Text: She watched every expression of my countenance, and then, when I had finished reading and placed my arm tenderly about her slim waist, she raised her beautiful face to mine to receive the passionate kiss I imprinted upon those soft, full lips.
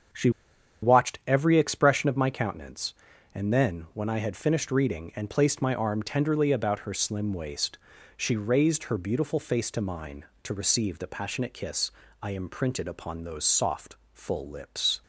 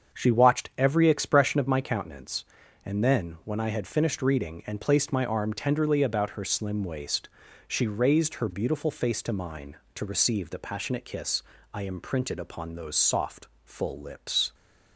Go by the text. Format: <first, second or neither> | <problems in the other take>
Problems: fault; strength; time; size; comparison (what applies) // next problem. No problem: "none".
second | starts louder than the rest; until 1.7 s; 7 dB; also in the second // pauses between "She" and "watched"; noticeable; at 0.3 s; 0.52 s long // pauses between "kiss" and "I"; slight; at 11.9 s; 0.32 s long; slight in the second